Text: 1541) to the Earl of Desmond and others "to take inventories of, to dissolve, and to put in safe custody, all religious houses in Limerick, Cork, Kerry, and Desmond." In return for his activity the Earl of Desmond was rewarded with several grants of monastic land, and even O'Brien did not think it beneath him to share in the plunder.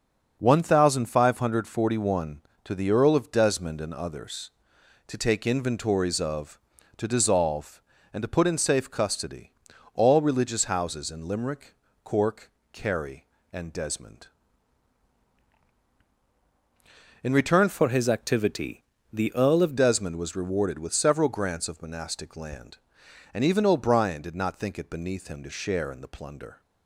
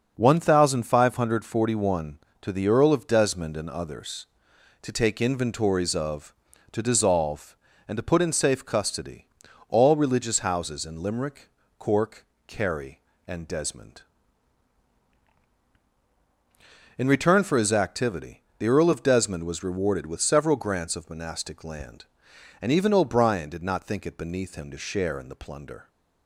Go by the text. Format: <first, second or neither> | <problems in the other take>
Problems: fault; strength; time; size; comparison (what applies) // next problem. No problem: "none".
second | starts louder than the rest; until 1.4 s; 6.5 dB; also in the second // changes voice from "for" to "of"; from 17.6 to 19.7 s; 2.1 s long // pauses between "activity" and "the"; slight; at 18.8 s; 0.26 s long; slight in the second